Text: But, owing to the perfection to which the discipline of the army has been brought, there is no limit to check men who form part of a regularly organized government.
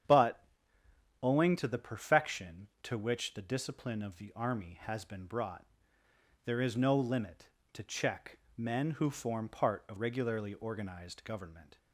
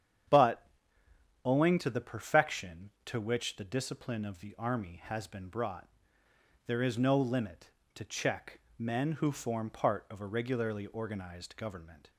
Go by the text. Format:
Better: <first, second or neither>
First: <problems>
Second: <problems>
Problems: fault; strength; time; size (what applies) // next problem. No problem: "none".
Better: second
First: starts louder than the rest; strong; until 1.8 s; 8.5 dB // pauses between "check" and "men"; slight; at 8.3 s; 0.20 s long // skips "a"; at 9.9 s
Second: starts louder than the rest; strong; until 2.0 s; 8.5 dB // pauses between "check" and "men"; slight; at 8.5 s; 0.20 s long